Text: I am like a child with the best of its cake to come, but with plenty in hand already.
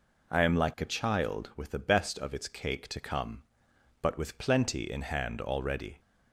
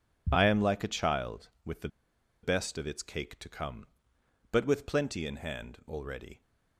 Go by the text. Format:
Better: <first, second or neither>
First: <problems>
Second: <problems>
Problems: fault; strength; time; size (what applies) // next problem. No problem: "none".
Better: first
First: none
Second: pauses between "the" and "best"; noticeable; at 1.8 s; 0.54 s long